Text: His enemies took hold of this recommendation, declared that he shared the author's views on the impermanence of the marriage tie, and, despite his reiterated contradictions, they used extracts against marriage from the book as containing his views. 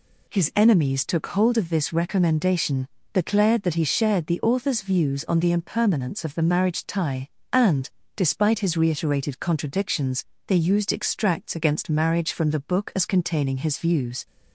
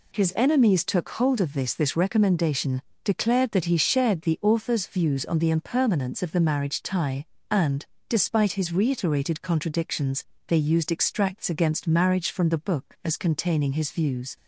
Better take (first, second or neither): first